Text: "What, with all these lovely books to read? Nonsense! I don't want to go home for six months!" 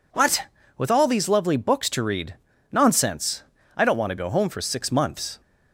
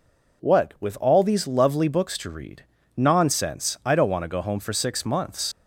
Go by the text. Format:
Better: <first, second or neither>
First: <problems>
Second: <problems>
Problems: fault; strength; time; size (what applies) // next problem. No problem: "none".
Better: first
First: none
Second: leaves "months" unfinished; at 5.5 s; 85 ms